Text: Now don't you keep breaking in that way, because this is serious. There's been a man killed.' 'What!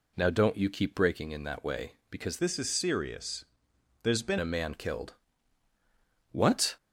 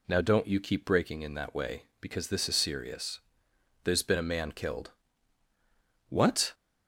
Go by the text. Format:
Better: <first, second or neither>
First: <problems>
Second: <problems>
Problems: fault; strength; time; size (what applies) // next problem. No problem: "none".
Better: second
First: changes voice from "this" to "been"; from 2.3 to 4.3 s; 2.0 s long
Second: none